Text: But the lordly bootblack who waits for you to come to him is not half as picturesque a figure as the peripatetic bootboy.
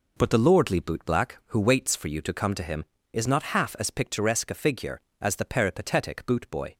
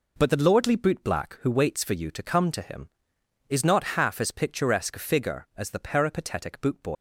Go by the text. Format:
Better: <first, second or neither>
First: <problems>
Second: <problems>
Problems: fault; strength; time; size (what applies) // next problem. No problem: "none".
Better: first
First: none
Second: leaves "bootboy" unfinished; at 6.9 s; 120 ms